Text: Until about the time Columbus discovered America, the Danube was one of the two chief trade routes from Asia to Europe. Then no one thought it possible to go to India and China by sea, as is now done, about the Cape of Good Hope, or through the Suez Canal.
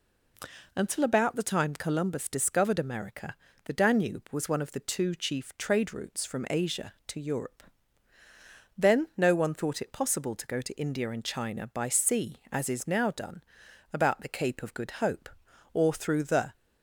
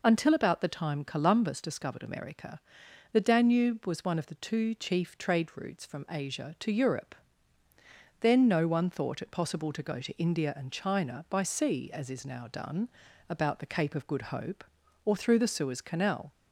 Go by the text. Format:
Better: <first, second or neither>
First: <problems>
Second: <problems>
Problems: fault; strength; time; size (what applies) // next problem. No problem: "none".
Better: second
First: stops before "Suez Canal"; at 16.5 s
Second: none